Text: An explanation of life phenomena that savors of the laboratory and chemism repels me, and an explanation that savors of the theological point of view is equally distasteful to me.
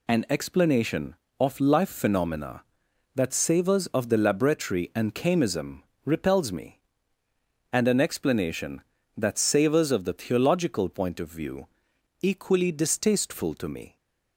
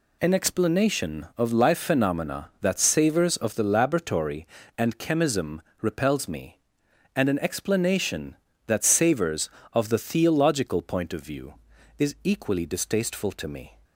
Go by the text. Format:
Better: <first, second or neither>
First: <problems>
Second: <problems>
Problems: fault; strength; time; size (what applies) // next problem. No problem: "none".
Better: second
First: pauses between "chemism" and "repels"; slight; at 5.8 s; 0.22 s long // skips "is"; at 11.9 s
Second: pauses between "chemism" and "repels"; slight; at 5.5 s; 0.22 s long